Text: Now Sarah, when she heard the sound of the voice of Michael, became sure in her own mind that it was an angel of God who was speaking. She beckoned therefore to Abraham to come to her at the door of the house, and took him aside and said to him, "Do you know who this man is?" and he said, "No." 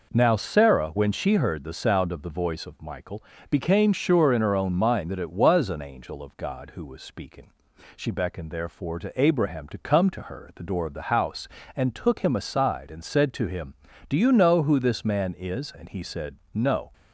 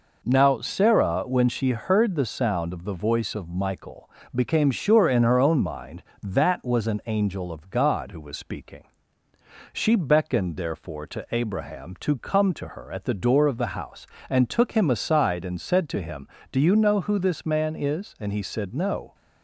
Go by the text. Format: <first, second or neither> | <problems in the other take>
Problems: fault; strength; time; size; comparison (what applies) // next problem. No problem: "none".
first | skips "it"; at 6.6 s